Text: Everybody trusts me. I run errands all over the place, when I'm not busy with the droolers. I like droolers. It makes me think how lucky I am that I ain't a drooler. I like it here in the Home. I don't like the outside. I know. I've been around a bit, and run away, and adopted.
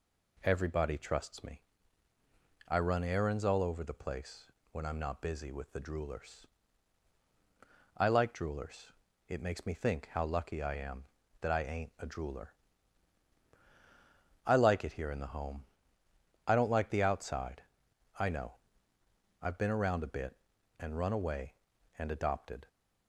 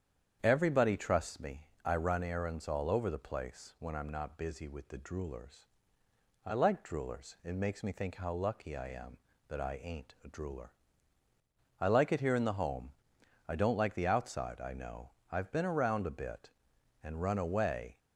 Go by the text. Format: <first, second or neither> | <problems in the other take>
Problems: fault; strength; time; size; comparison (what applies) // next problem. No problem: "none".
first | starts louder than the rest; strong; until 1.4 s; 8.5 dB // stops before "and adopted"; at 17.9 s